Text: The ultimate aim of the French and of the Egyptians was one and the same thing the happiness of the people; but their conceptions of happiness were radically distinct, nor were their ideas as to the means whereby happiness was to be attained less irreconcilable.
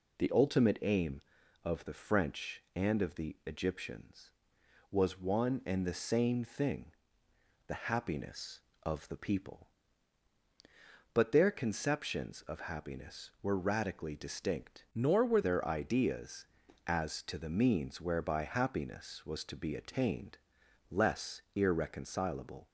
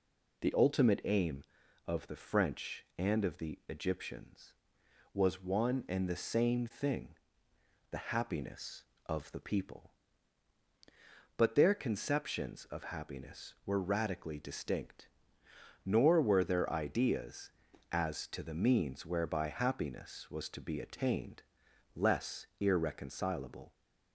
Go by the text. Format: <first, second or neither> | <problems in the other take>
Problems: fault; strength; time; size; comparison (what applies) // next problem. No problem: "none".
second | pauses between "thing" and "the"; noticeable; at 6.9 s; 0.74 s long; noticeable in the second // changes voice from "nor" to "were"; from 14.9 to 15.4 s; 0.5 s long // pauses between "attained" and "less"; noticeable; at 20.3 s; 0.54 s long; noticeable in the second